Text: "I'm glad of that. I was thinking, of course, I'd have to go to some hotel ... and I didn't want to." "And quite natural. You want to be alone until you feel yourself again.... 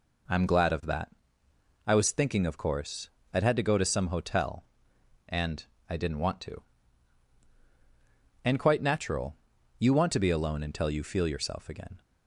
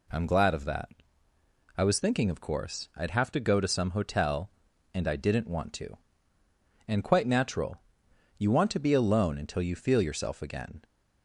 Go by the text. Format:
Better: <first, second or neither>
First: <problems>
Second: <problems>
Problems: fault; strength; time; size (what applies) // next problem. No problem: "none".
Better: second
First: says "had" for "have"; at 3.4 s // pauses between "and" and "I"; slight; at 5.6 s; 0.24 s long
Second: none